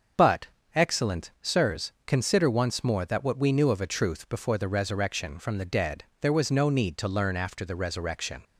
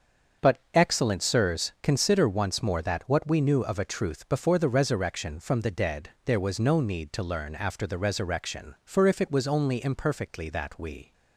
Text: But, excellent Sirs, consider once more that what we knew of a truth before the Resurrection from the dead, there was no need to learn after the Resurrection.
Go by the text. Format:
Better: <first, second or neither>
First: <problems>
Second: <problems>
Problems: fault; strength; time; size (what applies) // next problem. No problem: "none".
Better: first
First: starts louder than the rest; until 1.5 s; 6.5 dB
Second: starts louder than the rest; until 1.5 s; 6.5 dB // goes on to say "For if it was only imperfectly that we"; strong; from 8.8 s on; 2.2 s long